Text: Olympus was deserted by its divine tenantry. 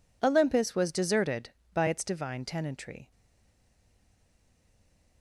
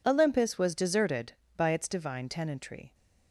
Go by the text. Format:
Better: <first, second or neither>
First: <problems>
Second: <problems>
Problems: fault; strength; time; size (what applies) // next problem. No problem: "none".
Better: second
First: stays silent after the last word; from 3.1 s on; 2.1 s long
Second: none